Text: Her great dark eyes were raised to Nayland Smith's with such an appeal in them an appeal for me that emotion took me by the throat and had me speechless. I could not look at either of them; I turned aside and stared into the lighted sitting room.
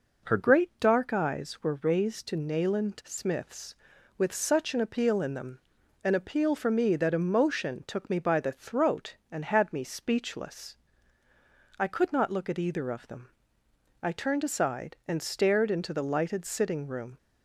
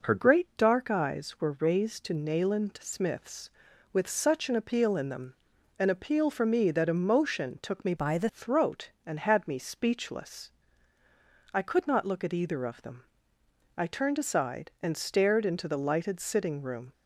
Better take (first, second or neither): first